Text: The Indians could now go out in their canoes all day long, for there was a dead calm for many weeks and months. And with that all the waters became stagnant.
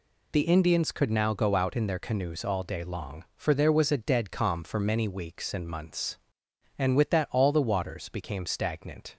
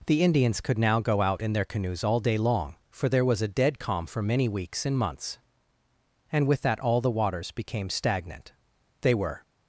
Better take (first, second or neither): first